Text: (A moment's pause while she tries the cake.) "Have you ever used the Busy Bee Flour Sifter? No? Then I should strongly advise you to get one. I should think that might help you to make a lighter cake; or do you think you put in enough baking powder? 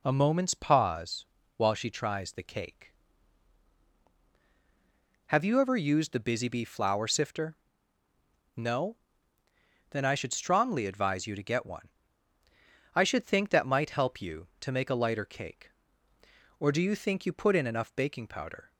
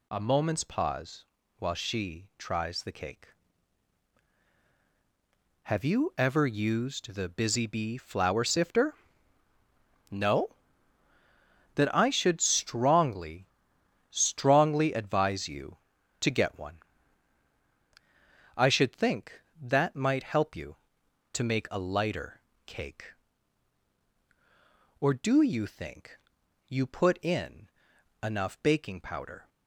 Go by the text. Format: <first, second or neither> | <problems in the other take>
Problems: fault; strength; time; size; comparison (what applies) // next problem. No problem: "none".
first | pauses between "pause" and "while"; slight; at 1.2 s; 0.34 s long; slight in the first // says "strongly" twice; at 14.0 s // pauses between "lighter" and "cake"; slight; at 22.3 s; 0.26 s long // pauses between "think" and "you"; noticeable; at 26.1 s; 0.52 s long // pauses between "in" and "enough"; noticeable; at 27.6 s; 0.54 s long